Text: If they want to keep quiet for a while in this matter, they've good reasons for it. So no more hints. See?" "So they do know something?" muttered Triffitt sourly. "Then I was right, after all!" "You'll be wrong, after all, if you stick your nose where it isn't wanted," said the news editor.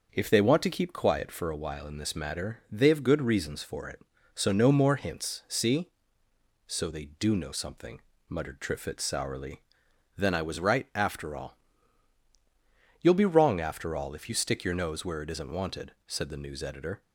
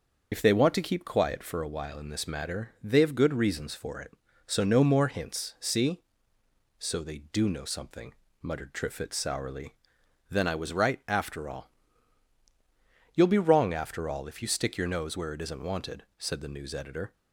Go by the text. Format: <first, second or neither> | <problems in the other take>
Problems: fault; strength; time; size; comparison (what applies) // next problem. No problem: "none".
first | loses the start of "If"; at 0.3 s; 85 ms // starts louder than the rest; until 1.3 s; 6 dB; also in the first